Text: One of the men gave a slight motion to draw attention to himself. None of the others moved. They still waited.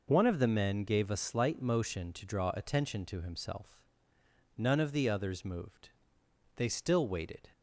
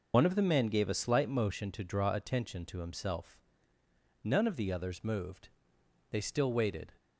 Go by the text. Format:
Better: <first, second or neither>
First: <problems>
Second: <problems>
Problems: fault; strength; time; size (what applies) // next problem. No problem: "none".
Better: first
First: none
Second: loses the start of "One"; at 0.1 s; 75 ms